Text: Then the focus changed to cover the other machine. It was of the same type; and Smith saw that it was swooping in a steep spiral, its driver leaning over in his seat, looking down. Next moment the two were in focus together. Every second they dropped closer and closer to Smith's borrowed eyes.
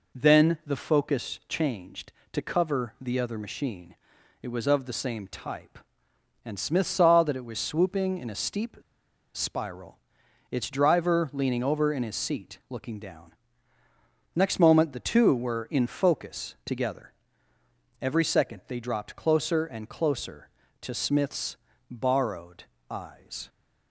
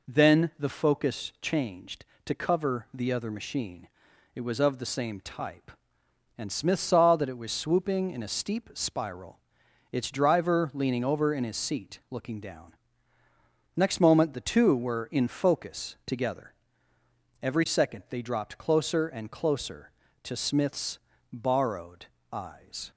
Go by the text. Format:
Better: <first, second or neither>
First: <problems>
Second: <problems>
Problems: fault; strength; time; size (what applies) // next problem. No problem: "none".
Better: second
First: pauses between "steep" and "spiral"; noticeable; at 8.7 s; 0.57 s long // pauses between "Smith's" and "borrowed"; slight; at 21.5 s; 0.34 s long // pauses between "borrowed" and "eyes"; slight; at 22.6 s; 0.24 s long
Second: pauses between "Smith's" and "borrowed"; slight; at 20.9 s; 0.34 s long // pauses between "borrowed" and "eyes"; slight; at 22.0 s; 0.24 s long